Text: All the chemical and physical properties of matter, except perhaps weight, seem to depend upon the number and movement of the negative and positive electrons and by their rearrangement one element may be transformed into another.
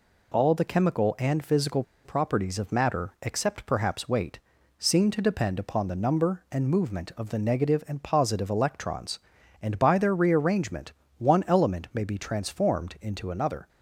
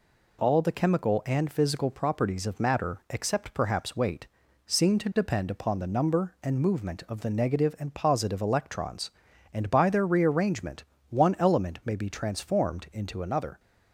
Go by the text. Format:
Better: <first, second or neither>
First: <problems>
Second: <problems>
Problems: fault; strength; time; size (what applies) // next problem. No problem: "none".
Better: second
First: pauses between "physical" and "properties"; slight; at 1.8 s; 0.21 s long // pauses between "rearrangement" and "one"; slight; at 10.9 s; 0.26 s long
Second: pauses between "rearrangement" and "one"; slight; at 10.8 s; 0.26 s long